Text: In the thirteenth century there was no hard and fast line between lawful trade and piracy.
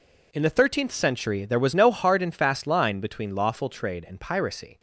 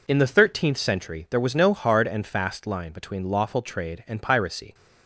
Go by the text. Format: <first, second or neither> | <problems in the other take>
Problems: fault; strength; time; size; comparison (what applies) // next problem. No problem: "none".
neither | none